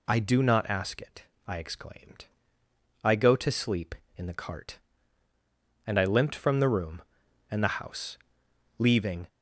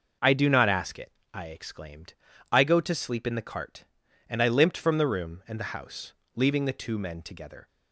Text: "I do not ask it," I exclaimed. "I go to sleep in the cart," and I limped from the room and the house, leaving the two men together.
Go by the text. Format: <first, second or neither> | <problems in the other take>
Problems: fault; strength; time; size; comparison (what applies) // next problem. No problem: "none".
second | stops before "the two men together"; at 9.2 s